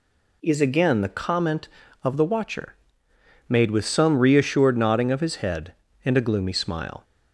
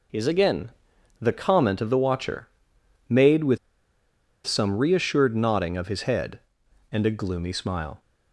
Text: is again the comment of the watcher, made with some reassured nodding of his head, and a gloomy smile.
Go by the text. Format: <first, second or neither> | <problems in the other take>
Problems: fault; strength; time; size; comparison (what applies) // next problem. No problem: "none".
first | pauses between "again" and "the"; noticeable; at 0.6 s; 0.50 s long // pauses between "with" and "some"; noticeable; at 3.5 s; 0.87 s long